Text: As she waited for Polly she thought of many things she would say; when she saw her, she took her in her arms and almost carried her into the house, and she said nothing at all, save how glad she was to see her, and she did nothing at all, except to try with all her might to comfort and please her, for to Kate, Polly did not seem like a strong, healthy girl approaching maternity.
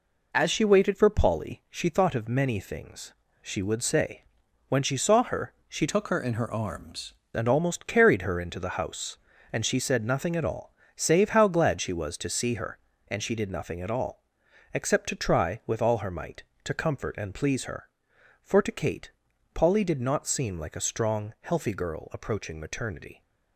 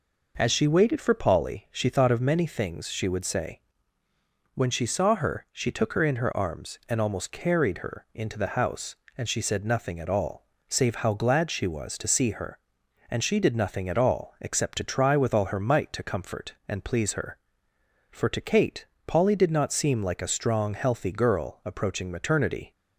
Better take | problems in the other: second | pauses between "things" and "she"; slight; at 3.1 s; 0.28 s long // changes voice from "took" to "arms"; from 5.8 to 7.1 s; 1.3 s long

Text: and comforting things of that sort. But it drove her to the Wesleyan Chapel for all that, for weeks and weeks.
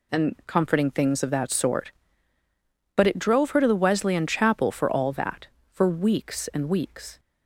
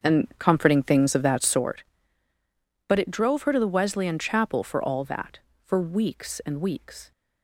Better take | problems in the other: first | starts louder than the rest; until 1.6 s; 7 dB

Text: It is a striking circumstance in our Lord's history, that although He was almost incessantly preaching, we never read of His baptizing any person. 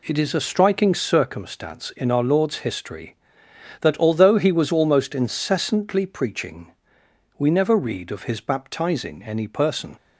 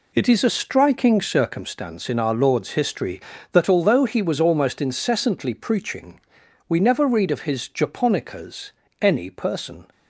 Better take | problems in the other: first | says "japonicas" for "baptizing"; at 7.6 s

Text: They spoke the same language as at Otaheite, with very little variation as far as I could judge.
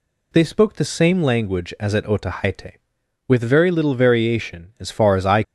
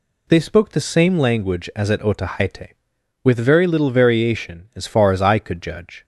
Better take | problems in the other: second | stops before "could judge"; at 5.4 s

